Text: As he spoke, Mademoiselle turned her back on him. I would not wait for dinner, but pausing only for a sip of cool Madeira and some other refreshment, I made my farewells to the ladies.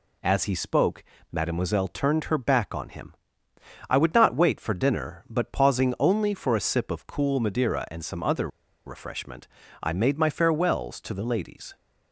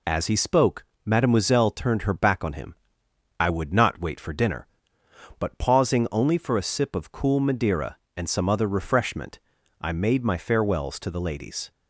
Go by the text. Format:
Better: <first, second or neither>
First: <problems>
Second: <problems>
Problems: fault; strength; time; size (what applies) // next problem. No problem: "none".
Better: second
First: pauses between "other" and "refreshment"; at 8.4 s; 0.38 s long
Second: none